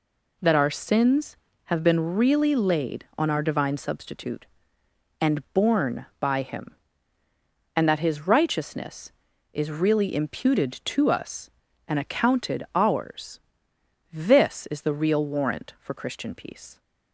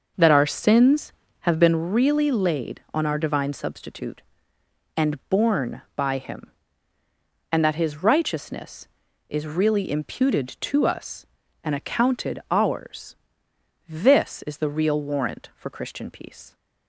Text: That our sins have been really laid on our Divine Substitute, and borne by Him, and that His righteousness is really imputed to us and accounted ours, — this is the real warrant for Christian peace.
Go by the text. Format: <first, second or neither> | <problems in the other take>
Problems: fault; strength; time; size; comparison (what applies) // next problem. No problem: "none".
first | starts louder than the rest; noticeable; until 1.8 s; 5.5 dB